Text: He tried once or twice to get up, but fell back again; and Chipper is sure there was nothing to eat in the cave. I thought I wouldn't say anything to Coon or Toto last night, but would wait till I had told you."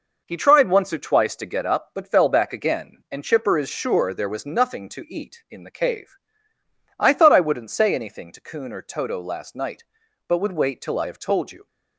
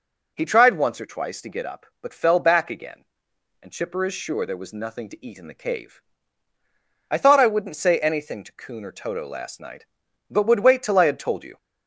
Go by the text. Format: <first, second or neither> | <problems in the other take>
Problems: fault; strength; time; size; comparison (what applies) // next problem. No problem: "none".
second | says "have" for "had"; at 11.0 s